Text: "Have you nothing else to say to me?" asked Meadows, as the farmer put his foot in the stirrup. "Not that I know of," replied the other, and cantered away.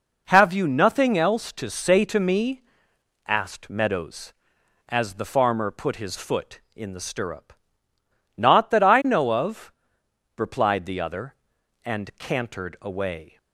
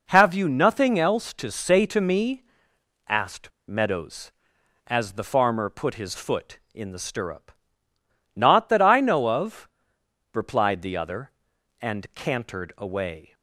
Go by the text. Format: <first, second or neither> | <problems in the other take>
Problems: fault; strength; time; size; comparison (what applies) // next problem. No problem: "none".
first | pauses between "asked" and "Meadows"; slight; at 3.5 s; 0.17 s long